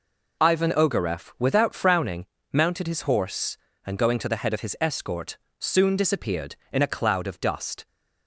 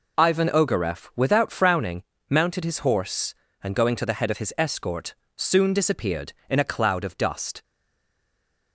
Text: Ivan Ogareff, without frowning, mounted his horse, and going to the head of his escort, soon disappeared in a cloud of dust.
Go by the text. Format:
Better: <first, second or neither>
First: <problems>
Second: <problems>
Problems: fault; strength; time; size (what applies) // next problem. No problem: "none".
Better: first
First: none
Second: stays silent after the last word; from 7.6 s on; 1.1 s long